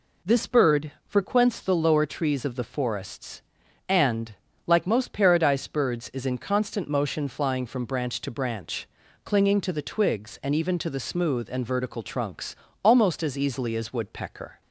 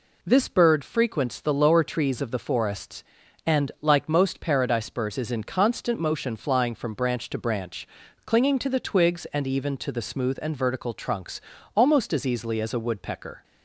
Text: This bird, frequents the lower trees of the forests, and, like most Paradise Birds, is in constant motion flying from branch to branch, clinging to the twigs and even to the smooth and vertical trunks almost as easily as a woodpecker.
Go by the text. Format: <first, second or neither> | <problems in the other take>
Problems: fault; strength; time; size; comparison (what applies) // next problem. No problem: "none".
second | pauses between "trunks" and "almost"; slight; at 12.5 s; 0.30 s long; slight in the second // skips "a"; at 13.9 s